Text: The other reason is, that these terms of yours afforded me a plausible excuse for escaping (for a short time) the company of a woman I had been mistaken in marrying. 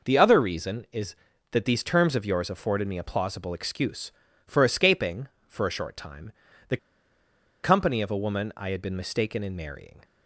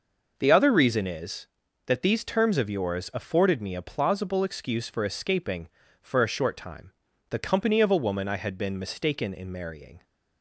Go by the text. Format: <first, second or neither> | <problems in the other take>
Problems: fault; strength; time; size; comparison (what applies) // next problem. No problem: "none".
second | pauses between "the" and "company"; noticeable; at 6.7 s; 0.85 s long